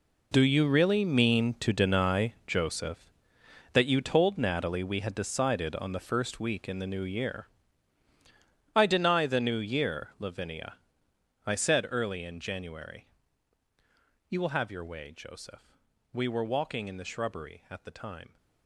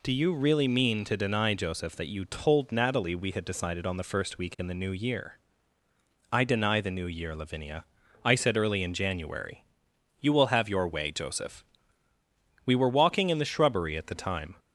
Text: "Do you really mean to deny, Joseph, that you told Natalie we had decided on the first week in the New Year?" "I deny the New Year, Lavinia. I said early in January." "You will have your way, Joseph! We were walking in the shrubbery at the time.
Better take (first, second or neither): second